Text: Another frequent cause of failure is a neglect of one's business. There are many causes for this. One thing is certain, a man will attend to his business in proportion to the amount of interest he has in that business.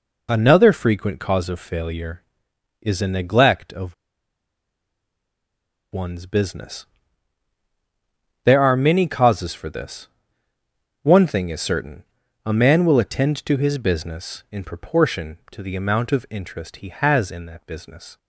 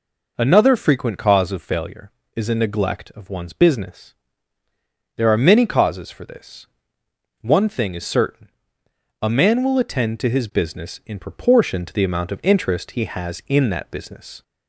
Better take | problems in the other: second | pauses between "of" and "one's"; strong; at 3.9 s; 1.9 s long

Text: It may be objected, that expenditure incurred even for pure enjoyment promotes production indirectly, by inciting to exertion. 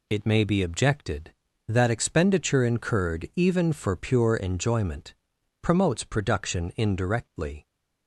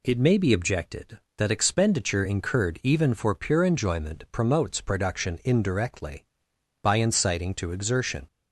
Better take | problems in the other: second | pauses between "enjoyment" and "promotes"; noticeable; at 5.1 s; 0.48 s long // stops before "by inciting to exertion"; at 7.6 s

